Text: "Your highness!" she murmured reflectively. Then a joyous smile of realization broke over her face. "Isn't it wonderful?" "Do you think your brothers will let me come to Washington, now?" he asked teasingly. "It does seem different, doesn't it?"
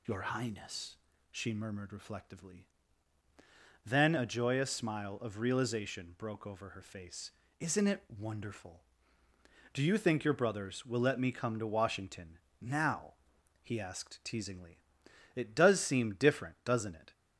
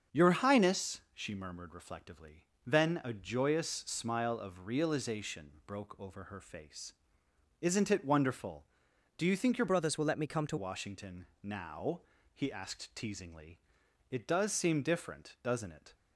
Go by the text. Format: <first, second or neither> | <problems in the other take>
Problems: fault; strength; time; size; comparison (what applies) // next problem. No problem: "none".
first | starts louder than the rest; until 1.2 s; 7 dB // changes voice from "brothers" to "to"; from 9.6 to 10.5 s; 0.9 s long